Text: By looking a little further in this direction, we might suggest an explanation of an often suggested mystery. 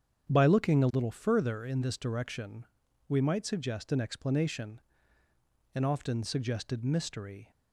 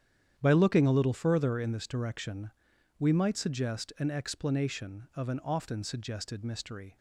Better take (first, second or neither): second